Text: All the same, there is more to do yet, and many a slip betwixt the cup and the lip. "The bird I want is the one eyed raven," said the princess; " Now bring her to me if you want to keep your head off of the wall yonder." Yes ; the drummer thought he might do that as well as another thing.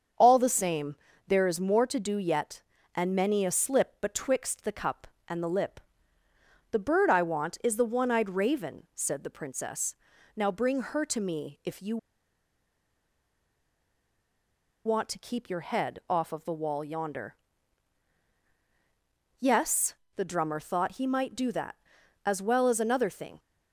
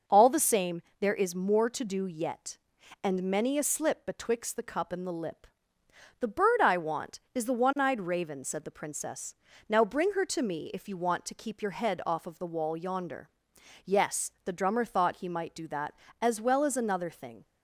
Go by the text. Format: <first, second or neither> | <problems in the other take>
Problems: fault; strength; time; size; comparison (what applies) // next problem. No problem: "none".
second | starts louder than the rest; strong; until 1.4 s; 7.5 dB // pauses between "you" and "want"; strong; at 11.9 s; 2.8 s long